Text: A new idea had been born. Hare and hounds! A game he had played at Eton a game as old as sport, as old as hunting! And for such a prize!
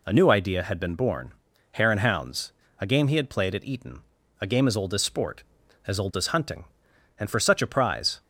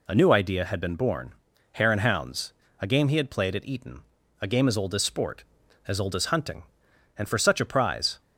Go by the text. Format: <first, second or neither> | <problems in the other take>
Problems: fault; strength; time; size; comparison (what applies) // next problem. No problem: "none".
neither | pauses between "Eton" and "a"; the same in both